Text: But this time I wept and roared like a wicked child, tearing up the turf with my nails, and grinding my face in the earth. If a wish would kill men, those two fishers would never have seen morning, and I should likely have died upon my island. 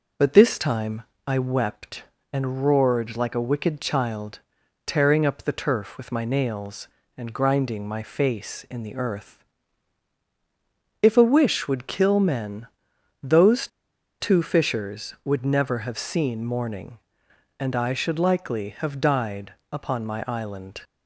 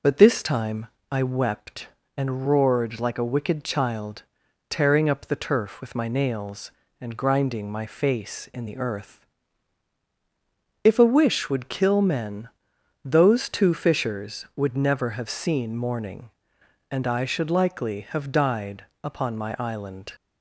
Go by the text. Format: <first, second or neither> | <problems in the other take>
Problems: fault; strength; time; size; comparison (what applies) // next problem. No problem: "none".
second | pauses between "time" and "I"; slight; at 1.0 s; 0.24 s long; slight in the second // pauses between "those" and "two"; noticeable; at 13.6 s; 0.53 s long // pauses between "died" and "upon"; slight; at 19.5 s; 0.18 s long; slight in the second